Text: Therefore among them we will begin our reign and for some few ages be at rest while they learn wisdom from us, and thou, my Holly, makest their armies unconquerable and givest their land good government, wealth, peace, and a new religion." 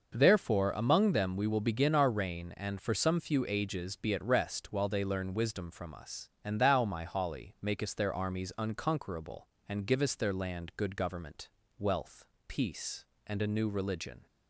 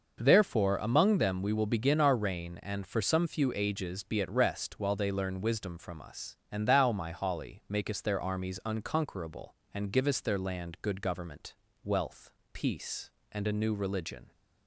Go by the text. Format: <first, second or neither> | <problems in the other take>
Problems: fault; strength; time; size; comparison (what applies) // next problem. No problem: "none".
neither | starts louder than the rest; noticeable; the same in both